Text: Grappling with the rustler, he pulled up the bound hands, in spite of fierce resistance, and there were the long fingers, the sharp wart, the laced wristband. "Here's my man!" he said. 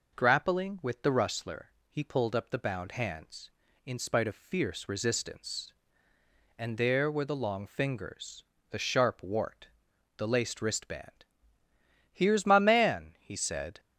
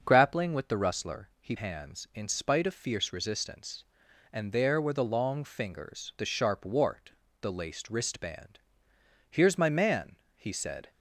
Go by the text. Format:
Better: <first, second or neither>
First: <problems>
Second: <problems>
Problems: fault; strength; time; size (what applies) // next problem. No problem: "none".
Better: first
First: none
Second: starts louder than the rest; until 1.0 s; 6.5 dB // skips "pulled up the bound"; at 1.5 s